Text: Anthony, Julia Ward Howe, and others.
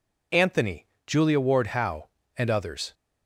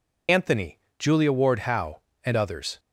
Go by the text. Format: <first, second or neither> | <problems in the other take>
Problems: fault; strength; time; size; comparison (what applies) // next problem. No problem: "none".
first | loses the start of "Anthony"; at 0.2 s; 45 ms